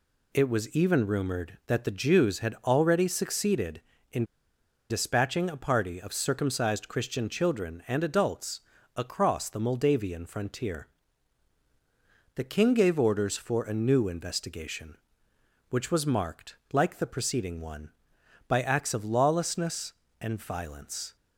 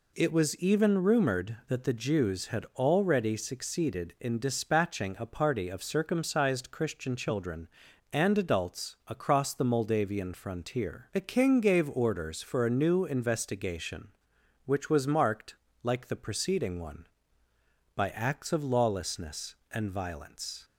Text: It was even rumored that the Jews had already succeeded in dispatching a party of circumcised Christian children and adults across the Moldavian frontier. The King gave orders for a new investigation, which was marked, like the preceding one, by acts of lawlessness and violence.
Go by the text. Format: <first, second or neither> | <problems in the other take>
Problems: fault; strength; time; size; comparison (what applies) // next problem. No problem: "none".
second | pauses between "in" and "dispatching"; noticeable; at 4.2 s; 0.66 s long // pauses between "adults" and "across"; slight; at 8.6 s; 0.34 s long